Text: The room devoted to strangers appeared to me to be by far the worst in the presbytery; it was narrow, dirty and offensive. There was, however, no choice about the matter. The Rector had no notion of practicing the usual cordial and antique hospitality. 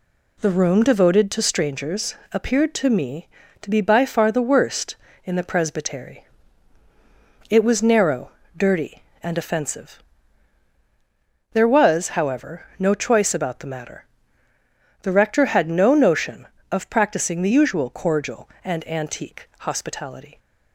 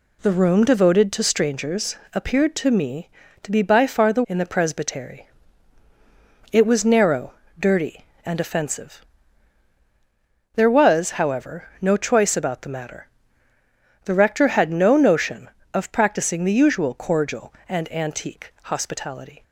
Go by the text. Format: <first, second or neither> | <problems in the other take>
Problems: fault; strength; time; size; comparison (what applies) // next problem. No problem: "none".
first | pauses between "strangers" and "appeared"; slight; at 1.9 s; 0.16 s long; slight in the first // skips "worst"; at 4.2 s